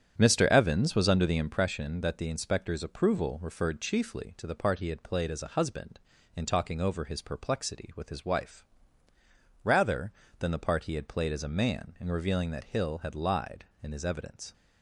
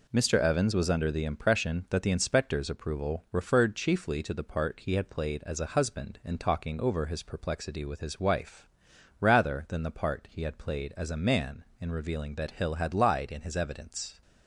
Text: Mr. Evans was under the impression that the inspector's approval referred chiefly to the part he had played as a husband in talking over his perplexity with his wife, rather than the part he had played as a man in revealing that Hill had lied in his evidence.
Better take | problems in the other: second | starts louder than the rest; strong; until 1.6 s; 9 dB

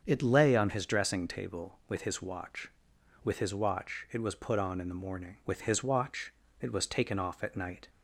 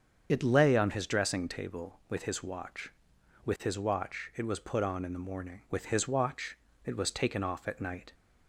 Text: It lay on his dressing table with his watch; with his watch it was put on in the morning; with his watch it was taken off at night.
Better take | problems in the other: first | loses the start of "It"; at 0.2 s; 55 ms // starts louder than the rest; strong; until 1.3 s; 7 dB; also in the first // pauses between "watch" and "it"; slight; at 6.5 s; 0.26 s long; slight in the first

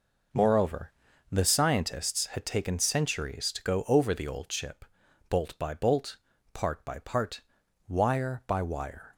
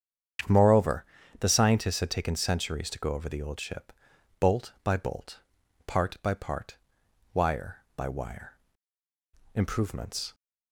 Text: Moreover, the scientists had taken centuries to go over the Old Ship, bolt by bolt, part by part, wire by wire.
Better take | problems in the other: first | starts louder than the rest; strong; until 1.8 s; 8 dB // goes on to say "Improvements"; noticeable; from 9.5 s on; 0.80 s long

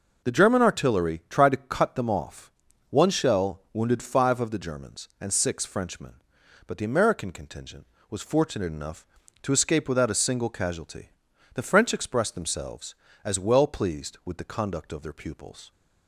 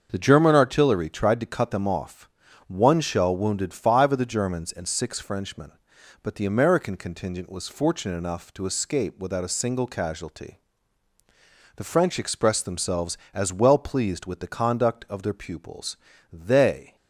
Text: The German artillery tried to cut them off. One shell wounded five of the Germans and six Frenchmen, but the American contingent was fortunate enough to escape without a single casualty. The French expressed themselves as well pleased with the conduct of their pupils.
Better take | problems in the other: first | starts louder than the rest; until 1.1 s; 6.5 dB // goes on to say "They"; noticeable; from 16.3 s on; 0.62 s long

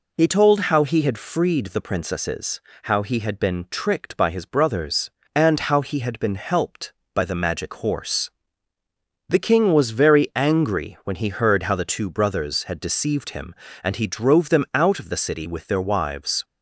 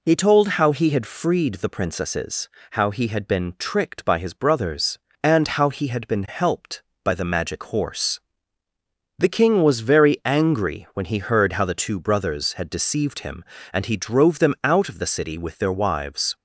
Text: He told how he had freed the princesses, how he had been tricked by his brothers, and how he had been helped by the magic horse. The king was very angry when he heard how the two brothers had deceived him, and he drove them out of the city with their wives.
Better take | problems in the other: neither | none

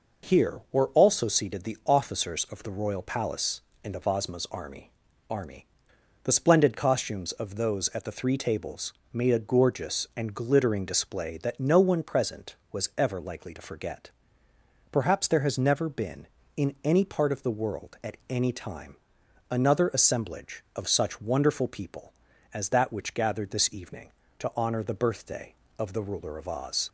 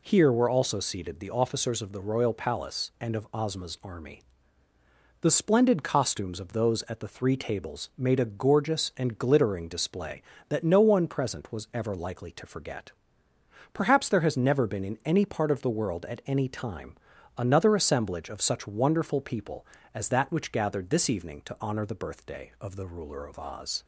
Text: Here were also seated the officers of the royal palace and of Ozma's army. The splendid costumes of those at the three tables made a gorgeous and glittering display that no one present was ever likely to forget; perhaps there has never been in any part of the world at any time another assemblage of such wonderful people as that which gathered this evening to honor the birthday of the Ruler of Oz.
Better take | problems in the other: second | says "army" twice; at 5.3 s // pauses between "tables" and "made"; slight; at 8.9 s; 0.18 s long // pauses between "time" and "another"; noticeable; at 18.9 s; 0.54 s long; also in the second

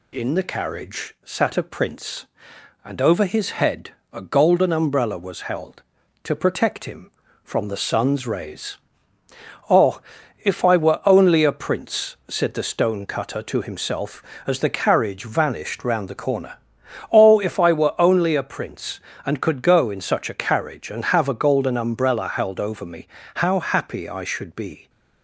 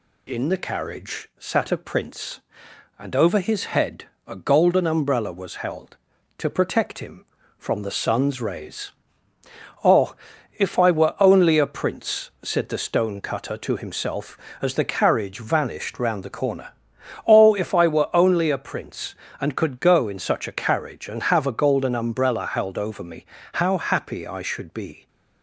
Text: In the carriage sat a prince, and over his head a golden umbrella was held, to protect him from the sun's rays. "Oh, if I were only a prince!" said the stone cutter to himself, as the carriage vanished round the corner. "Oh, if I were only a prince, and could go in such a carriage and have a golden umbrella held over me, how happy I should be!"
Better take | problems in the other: neither | pauses between "head" and "a"; slight; the same in both

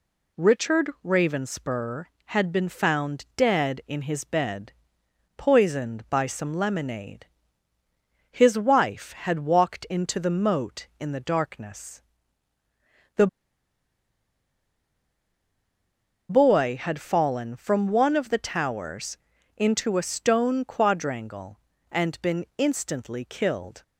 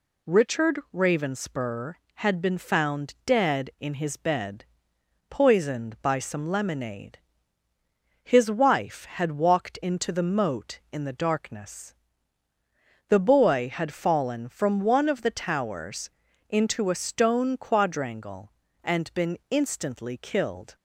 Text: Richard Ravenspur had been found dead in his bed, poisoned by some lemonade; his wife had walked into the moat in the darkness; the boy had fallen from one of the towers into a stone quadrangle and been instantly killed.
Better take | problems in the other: second | pauses between "Richard" and "Ravenspur"; slight; at 0.8 s; 0.16 s long; slight in the second // pauses between "the" and "boy"; strong; at 13.2 s; 3.0 s long // pauses between "towers" and "into"; at 19.1 s; 0.40 s long; also in the second

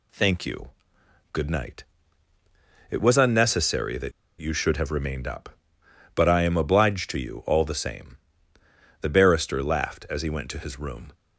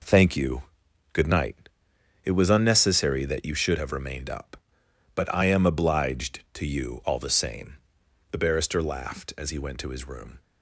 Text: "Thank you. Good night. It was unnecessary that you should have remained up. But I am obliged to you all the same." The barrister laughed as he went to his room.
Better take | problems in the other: second | pauses between "that" and "you"; slight; at 4.1 s; 0.28 s long

